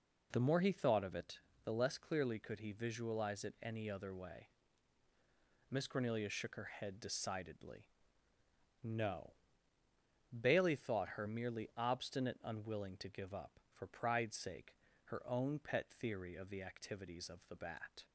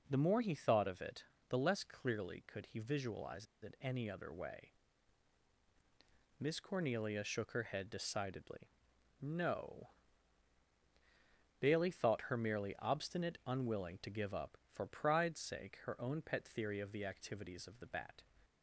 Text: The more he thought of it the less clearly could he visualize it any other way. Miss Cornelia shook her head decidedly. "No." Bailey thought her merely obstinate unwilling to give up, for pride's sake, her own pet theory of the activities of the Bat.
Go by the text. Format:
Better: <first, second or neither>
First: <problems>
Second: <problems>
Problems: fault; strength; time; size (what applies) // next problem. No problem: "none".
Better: first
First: pauses between "it" and "the"; slight; at 1.3 s; 0.26 s long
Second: pauses between "it" and "the"; slight; at 1.2 s; 0.26 s long // pauses between "visualize" and "it"; slight; at 3.4 s; 0.16 s long